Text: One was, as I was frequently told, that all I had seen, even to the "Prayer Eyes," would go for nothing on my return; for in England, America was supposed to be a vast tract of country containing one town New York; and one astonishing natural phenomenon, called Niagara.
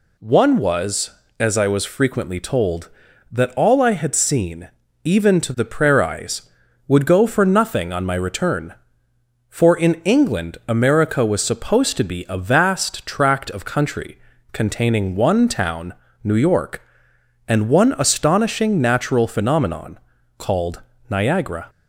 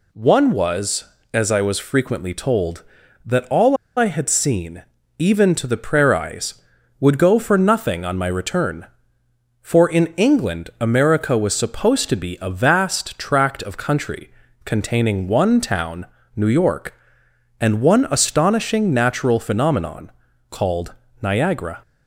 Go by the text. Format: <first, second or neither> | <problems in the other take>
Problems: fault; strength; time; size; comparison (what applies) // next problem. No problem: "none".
first | pauses between "all" and "I"; slight; at 3.7 s; 0.21 s long // pauses between "country" and "containing"; slight; at 14.2 s; 0.34 s long; slight in the first // pauses between "town" and "New"; slight; at 16.0 s; 0.28 s long; slight in the first // pauses between "called" and "Niagara"; slight; at 20.9 s; 0.28 s long; slight in the first